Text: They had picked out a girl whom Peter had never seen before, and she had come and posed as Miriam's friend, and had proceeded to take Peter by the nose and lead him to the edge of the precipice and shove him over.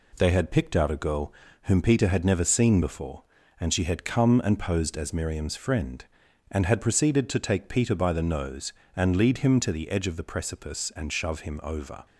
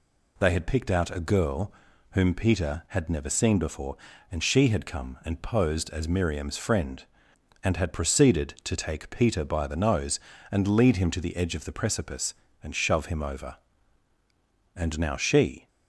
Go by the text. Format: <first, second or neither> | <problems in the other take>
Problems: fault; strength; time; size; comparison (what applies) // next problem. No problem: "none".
first | pauses between "girl" and "whom"; at 1.7 s; 0.40 s long; slight in the first // goes on to say "And now she"; noticeable; from 14.7 s on; 0.92 s long